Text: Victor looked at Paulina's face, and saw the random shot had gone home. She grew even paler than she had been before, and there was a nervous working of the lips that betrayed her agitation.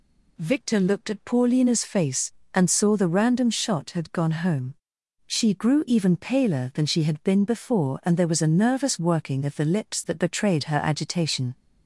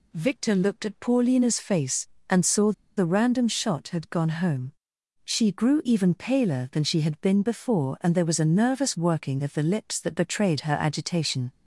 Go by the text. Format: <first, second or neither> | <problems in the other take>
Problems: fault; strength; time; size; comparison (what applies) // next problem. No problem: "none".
first | pauses between "saw" and "the"; slight; at 2.7 s; 0.24 s long